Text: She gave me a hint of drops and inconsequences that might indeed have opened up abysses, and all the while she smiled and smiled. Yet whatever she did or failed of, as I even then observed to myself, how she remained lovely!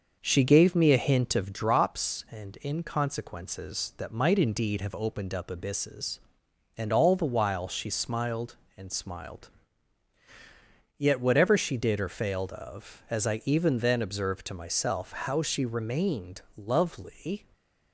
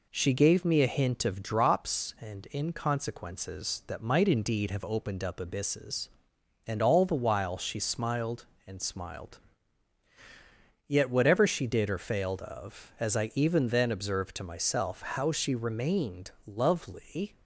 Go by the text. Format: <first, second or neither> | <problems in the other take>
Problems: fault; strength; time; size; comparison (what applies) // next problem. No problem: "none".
second | starts louder than the rest; noticeable; until 1.6 s; 6 dB // pauses between "remained" and "lovely"; slight; at 16.4 s; 0.16 s long; slight in the second // stays silent after the last word; slight; from 17.3 s on; 0.6 s long